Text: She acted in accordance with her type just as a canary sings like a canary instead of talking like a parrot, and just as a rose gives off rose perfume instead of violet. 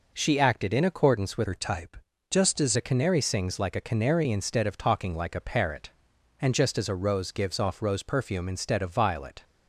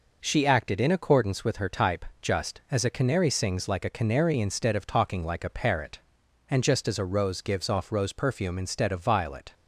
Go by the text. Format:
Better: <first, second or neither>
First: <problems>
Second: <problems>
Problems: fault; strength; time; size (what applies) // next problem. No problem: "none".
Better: second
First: changes voice from "her" to "as"; from 1.4 to 2.7 s; 1.3 s long // pauses between "type" and "just"; slight; at 1.9 s; 0.34 s long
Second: pauses between "type" and "just"; slight; at 2.0 s; 0.16 s long